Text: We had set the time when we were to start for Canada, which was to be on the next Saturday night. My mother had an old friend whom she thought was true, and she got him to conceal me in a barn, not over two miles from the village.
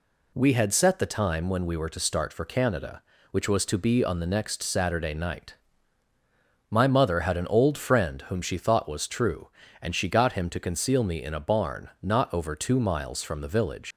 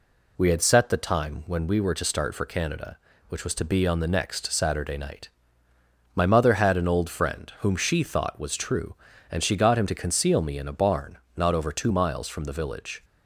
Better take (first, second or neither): second